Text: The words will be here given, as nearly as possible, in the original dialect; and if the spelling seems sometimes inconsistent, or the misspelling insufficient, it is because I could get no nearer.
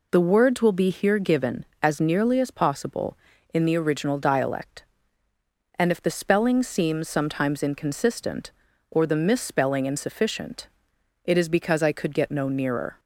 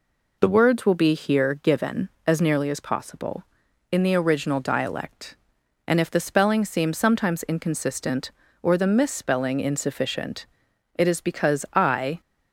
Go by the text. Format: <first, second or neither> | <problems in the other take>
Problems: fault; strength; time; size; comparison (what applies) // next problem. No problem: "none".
first | stops before "could get no nearer"; at 12.2 s